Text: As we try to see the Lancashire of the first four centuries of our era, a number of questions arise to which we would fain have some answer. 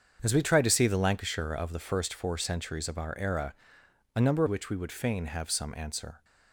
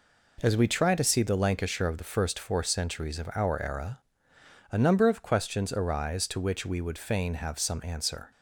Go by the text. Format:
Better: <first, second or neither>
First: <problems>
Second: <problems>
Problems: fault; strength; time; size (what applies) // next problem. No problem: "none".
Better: second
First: starts louder than the rest; until 1.2 s; 7 dB // skips "of questions arise to"; at 4.4 s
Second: none